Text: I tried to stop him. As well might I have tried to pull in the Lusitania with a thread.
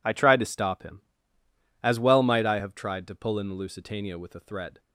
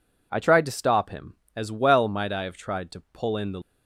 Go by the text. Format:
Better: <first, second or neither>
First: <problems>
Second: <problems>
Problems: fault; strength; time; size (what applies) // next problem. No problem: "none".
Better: first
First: none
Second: stops before "Lusitania with a thread"; at 3.6 s